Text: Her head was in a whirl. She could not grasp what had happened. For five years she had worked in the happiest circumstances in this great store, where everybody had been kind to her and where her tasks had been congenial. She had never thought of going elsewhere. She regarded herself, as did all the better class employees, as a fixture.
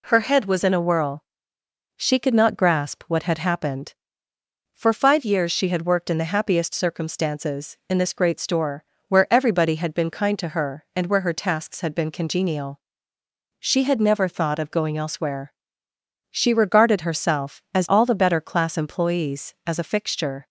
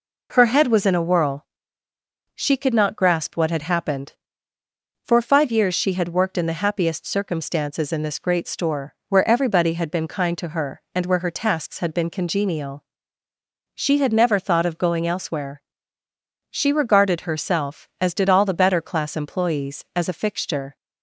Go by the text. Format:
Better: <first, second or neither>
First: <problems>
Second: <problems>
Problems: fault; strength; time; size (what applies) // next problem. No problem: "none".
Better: second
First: skips "did"; at 17.8 s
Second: none